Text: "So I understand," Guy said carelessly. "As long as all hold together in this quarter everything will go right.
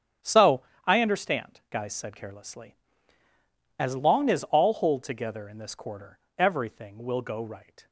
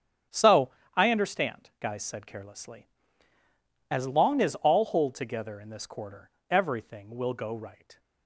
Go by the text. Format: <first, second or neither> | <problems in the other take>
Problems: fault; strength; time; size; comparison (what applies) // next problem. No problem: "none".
neither | starts louder than the rest; strong; the same in both // pauses between "So" and "I"; slight; the same in both // pauses between "quarter" and "everything"; slight; the same in both